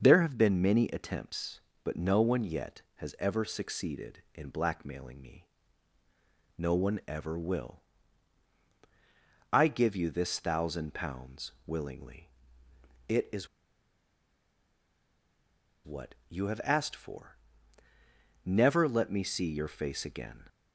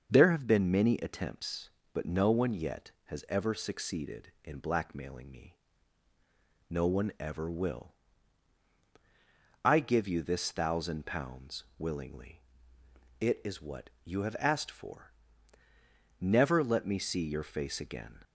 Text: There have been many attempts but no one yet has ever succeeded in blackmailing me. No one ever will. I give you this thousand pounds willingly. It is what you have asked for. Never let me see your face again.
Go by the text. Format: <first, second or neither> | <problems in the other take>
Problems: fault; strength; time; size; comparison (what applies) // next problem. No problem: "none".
second | starts louder than the rest; until 1.0 s; 6.5 dB; also in the second // pauses between "pounds" and "willingly"; slight; at 11.5 s; 0.16 s long; slight in the second // pauses between "is" and "what"; strong; at 13.4 s; 2.3 s long // pauses between "what" and "you"; slight; at 16.1 s; 0.16 s long; slight in the second